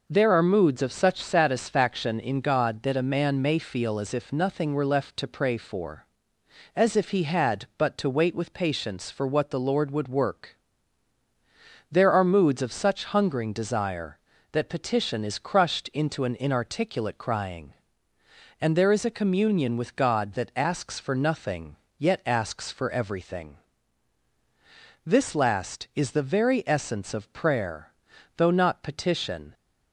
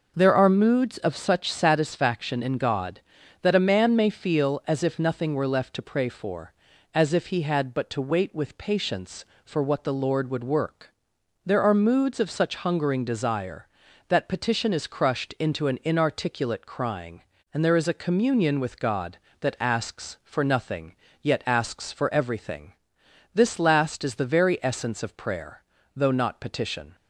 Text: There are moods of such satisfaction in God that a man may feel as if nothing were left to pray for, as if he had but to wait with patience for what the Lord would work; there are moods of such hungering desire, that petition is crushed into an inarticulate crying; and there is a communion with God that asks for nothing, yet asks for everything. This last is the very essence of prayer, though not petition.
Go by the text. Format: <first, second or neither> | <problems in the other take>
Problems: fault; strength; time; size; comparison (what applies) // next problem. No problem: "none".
neither | none